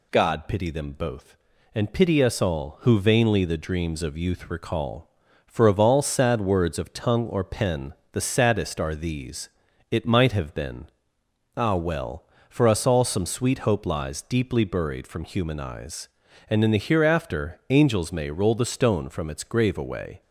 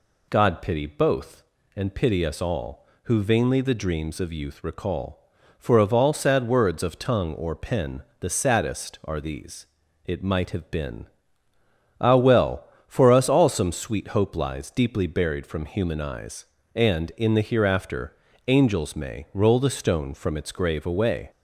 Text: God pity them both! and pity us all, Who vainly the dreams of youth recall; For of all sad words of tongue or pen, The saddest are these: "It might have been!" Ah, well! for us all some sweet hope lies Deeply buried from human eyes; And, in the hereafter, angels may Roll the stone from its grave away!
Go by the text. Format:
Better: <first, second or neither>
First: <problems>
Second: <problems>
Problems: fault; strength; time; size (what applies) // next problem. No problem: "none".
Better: first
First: none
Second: skips "them"; at 0.8 s